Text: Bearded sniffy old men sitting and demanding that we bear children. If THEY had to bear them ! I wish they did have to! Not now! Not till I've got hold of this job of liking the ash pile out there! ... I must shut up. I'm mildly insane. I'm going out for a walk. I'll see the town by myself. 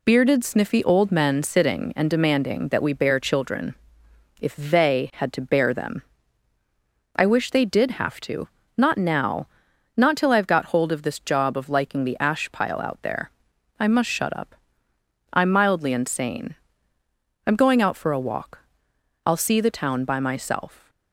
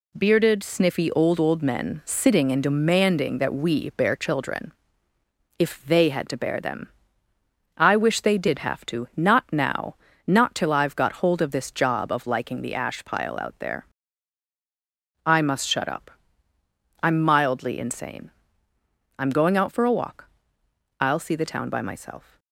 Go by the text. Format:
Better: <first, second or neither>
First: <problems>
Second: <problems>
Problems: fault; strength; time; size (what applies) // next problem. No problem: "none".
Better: first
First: none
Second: says "old" twice; at 1.3 s